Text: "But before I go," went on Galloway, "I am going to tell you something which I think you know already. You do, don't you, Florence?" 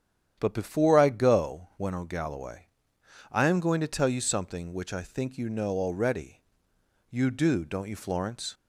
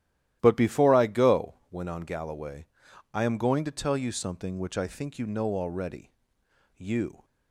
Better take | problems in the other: first | starts louder than the rest; strong; until 1.4 s; 13 dB; strong in the first // stops before "do don't you Florence"; at 7.2 s

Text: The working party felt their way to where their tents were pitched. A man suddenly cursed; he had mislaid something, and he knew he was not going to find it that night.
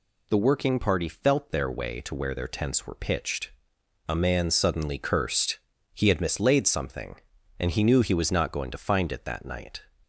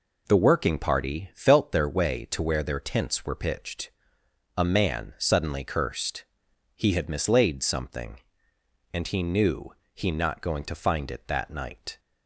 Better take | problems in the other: first | pauses between "knew" and "he"; slight; at 9.7 s; 0.20 s long // skips "was"; at 10.0 s

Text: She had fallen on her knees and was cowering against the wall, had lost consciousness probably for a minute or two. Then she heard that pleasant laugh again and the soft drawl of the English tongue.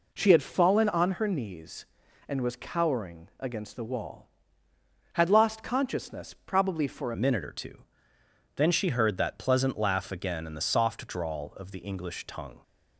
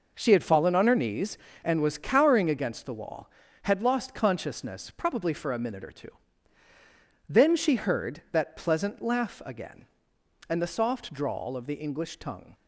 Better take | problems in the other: second | changes voice at "minute"; from 7.1 s on; 5.5 s long

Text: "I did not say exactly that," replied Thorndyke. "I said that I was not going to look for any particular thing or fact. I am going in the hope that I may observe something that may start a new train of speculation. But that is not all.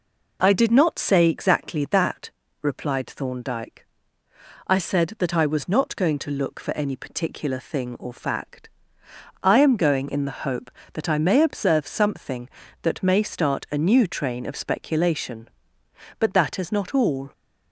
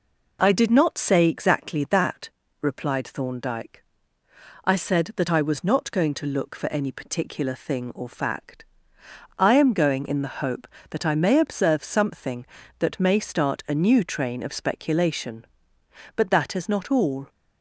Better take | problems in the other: neither | none

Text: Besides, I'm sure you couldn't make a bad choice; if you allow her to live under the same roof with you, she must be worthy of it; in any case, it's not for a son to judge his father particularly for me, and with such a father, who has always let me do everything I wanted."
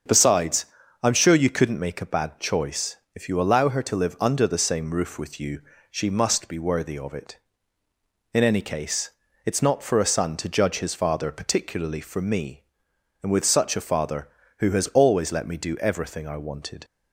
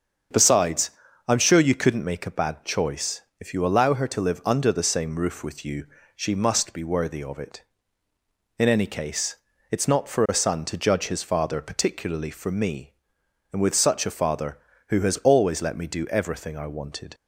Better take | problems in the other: neither | starts louder than the rest; the same in both

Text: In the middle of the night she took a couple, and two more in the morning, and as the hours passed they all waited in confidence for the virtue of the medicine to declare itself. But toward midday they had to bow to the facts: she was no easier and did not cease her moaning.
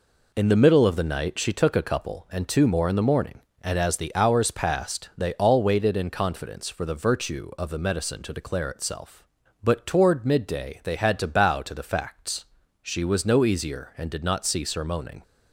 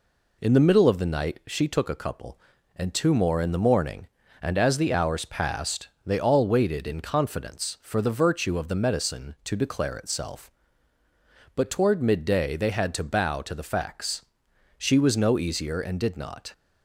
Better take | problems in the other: first | pauses between "passed" and "they"; slight; at 5.8 s; 0.18 s long // stops before "cease her moaning"; at 16.5 s

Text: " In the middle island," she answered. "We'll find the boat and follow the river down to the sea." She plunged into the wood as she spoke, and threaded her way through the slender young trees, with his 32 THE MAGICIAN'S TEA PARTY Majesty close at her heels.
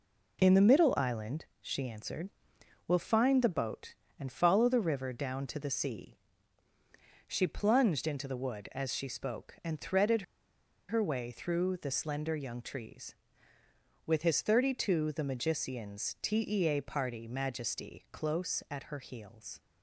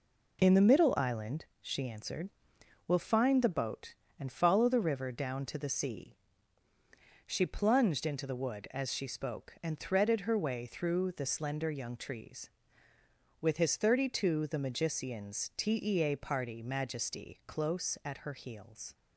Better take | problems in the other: second | pauses between "threaded" and "her"; noticeable; at 10.2 s; 0.66 s long

